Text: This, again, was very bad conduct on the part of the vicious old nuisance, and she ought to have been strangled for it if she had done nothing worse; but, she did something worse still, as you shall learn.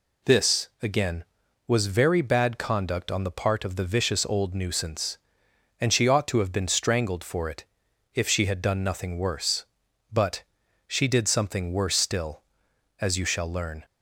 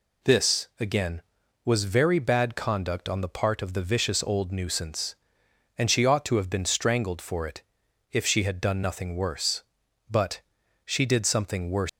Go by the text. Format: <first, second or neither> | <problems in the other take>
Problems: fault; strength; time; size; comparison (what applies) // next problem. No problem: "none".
first | pauses between "it" and "if"; noticeable; at 7.6 s; 0.48 s long; noticeable in the first // stops before "still as you shall learn"; at 11.8 s